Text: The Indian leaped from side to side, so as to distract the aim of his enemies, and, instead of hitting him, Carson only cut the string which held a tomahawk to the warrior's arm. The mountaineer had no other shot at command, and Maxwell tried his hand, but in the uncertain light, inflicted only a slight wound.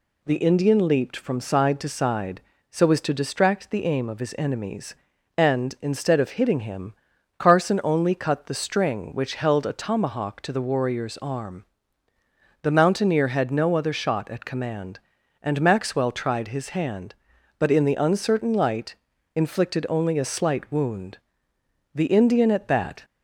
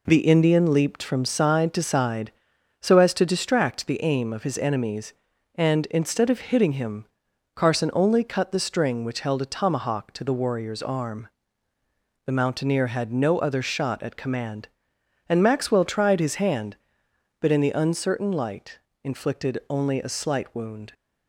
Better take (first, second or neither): second